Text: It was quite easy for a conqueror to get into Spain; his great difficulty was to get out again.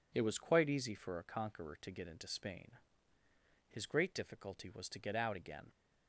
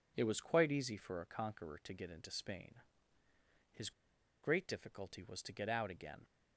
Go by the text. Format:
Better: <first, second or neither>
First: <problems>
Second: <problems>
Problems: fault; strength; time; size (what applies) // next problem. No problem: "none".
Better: first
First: none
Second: pauses between "his" and "great"; noticeable; at 3.9 s; 0.52 s long